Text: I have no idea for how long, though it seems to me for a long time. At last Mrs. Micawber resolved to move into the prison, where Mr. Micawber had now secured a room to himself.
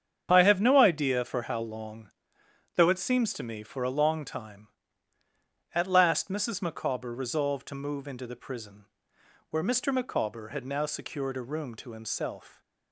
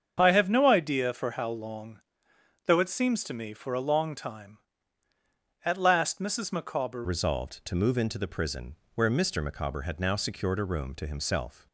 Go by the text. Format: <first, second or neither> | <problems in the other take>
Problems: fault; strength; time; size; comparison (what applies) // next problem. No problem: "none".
first | starts louder than the rest; strong; until 1.2 s; 7 dB; strong in the first // changes voice at "resolved"; from 7.0 s on; 4.6 s long